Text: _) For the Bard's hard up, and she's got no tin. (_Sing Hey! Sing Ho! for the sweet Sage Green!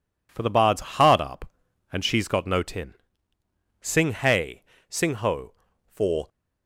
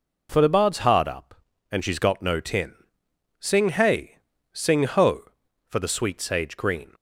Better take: second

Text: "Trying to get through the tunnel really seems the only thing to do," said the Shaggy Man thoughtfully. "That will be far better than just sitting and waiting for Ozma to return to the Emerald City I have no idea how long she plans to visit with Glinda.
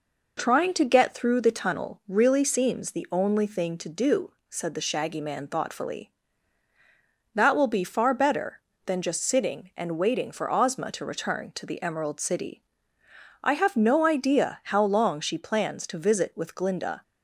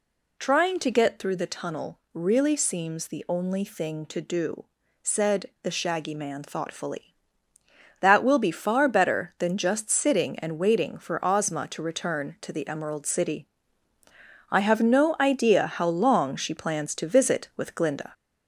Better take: first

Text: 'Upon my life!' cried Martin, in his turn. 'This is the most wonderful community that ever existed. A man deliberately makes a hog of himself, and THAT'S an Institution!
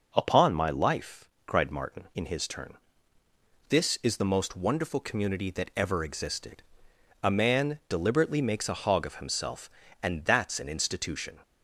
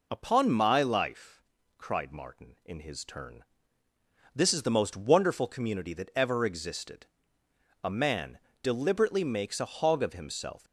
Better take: first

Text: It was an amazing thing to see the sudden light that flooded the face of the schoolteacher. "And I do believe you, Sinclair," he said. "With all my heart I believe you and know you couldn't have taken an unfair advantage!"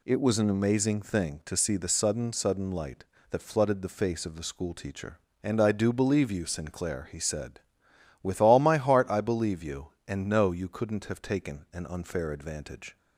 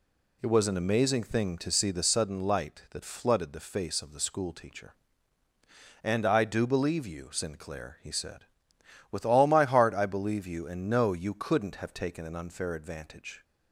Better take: second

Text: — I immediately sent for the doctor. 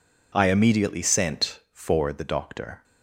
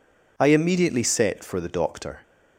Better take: first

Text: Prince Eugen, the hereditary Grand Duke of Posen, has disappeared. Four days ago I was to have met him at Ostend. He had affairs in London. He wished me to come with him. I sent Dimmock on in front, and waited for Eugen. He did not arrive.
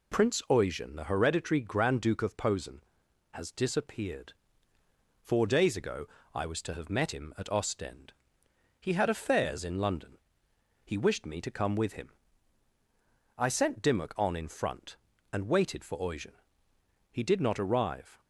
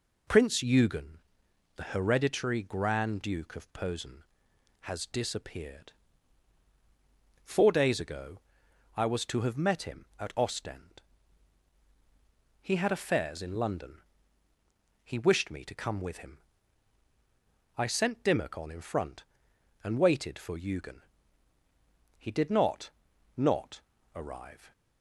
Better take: first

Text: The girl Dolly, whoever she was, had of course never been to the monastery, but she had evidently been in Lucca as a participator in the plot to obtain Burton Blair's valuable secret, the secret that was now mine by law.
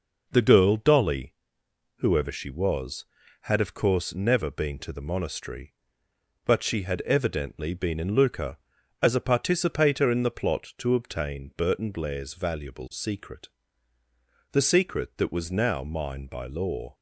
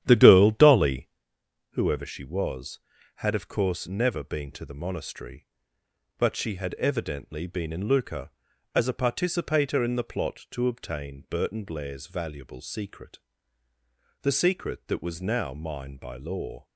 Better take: first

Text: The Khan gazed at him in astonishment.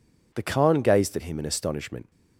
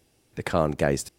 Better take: first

